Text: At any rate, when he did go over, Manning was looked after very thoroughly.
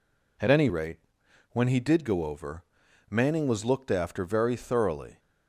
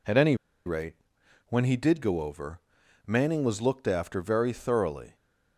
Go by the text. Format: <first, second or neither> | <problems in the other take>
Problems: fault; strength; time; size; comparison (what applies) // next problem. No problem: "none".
first | pauses between "any" and "rate"; slight; at 0.3 s; 0.31 s long